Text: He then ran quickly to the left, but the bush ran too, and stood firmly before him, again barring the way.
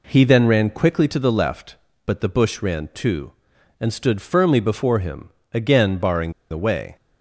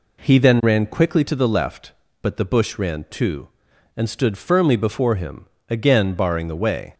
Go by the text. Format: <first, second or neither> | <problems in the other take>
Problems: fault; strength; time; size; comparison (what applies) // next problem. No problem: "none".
second | pauses between "barring" and "the"; slight; at 6.3 s; 0.19 s long